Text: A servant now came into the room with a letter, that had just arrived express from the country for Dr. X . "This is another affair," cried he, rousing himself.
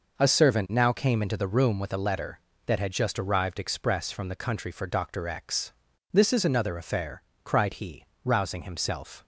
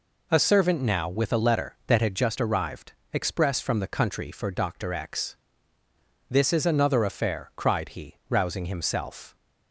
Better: first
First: none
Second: skips "came into the room"; at 1.0 s // pauses between "arrived" and "express"; slight; at 2.9 s; 0.18 s long

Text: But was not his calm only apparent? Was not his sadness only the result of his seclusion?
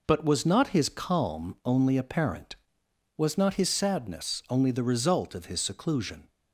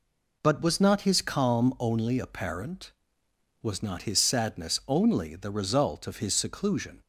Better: neither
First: none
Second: none

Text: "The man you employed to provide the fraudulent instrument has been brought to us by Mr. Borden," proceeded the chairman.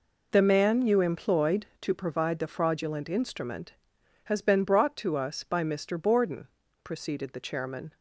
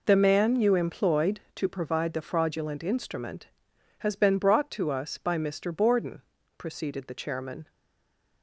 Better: first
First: none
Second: stays silent after the last word; slight; from 7.6 s on; 0.8 s long

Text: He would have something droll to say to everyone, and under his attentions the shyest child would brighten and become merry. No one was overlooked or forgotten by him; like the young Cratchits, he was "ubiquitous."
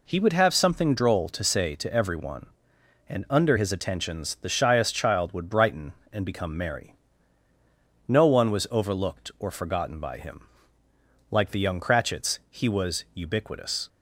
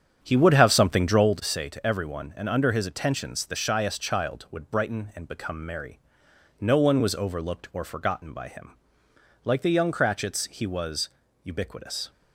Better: first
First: none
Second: starts louder than the rest; strong; until 1.5 s; 8.5 dB // pauses between "was" and "ubiquitous"; slight; at 11.0 s; 0.34 s long

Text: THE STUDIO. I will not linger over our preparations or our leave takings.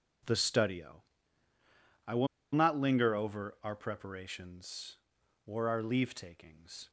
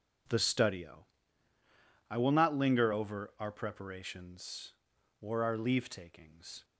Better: second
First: pauses between "will" and "not"; slight; at 2.2 s; 0.28 s long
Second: none

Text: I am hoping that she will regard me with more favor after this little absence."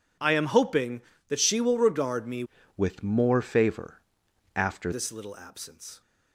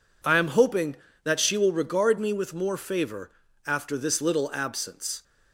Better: second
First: changes voice from "with" to "after"; from 2.7 to 4.9 s; 2.2 s long // pauses between "favor" and "after"; noticeable; at 4.0 s; 0.54 s long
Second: pauses between "favor" and "after"; slight; at 3.3 s; 0.34 s long

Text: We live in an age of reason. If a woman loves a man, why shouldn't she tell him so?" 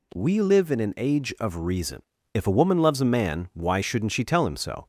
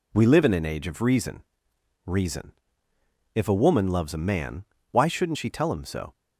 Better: first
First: none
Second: says "reason" twice; at 2.0 s

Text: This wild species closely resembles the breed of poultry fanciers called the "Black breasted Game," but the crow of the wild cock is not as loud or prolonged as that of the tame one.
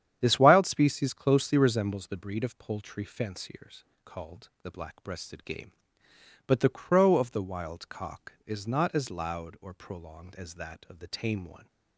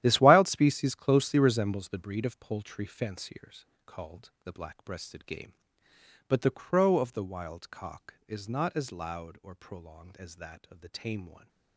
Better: first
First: starts louder than the rest; strong; until 1.2 s; 9.5 dB // pauses between "fanciers" and "called"; slight; at 3.8 s; 0.22 s long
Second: gets quieter; strong; throughout; 14 dB // starts louder than the rest; strong; until 1.0 s; 12.5 dB // pauses between "fanciers" and "called"; slight; at 3.6 s; 0.22 s long

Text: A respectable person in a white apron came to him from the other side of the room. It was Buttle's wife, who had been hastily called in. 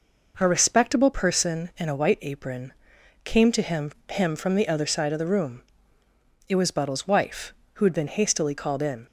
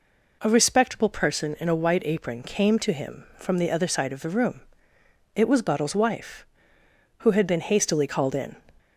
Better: second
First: pauses between "apron" and "came"; noticeable; at 2.7 s; 0.50 s long // says "him" twice; at 4.1 s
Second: none

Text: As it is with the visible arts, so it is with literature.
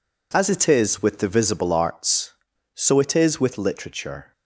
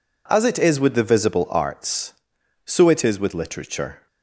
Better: neither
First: none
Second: none

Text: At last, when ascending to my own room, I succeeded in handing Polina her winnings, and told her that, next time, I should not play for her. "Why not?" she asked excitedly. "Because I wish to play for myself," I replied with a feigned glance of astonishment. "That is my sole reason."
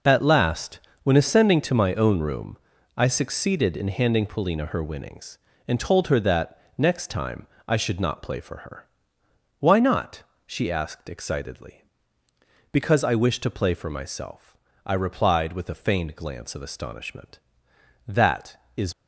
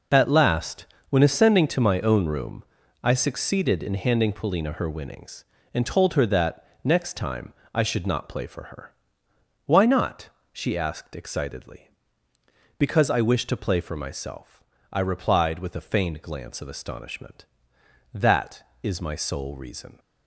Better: second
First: stops before "my sole reason"; at 18.9 s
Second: none

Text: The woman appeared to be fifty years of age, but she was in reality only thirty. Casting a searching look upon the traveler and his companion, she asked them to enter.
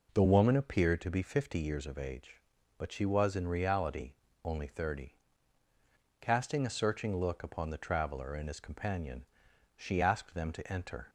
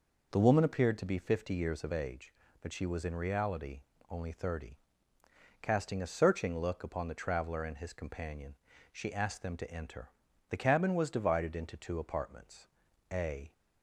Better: first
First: pauses between "reality" and "only"; slight; at 4.1 s; 0.30 s long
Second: pauses between "reality" and "only"; slight; at 3.8 s; 0.30 s long // goes on to say "The cabin was divided into two apartments a"; strong; from 10.5 s on; 3.0 s long

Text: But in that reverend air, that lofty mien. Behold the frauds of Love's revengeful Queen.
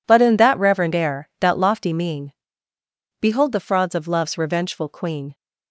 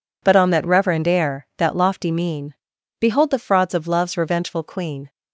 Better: first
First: none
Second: says "on" for "in"; at 0.3 s

